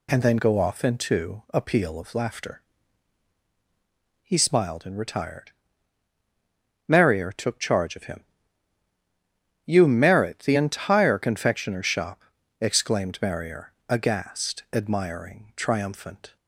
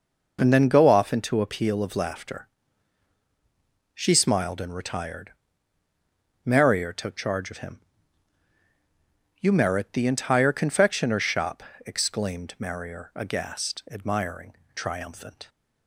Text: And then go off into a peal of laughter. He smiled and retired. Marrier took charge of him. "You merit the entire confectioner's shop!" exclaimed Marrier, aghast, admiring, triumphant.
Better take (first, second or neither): first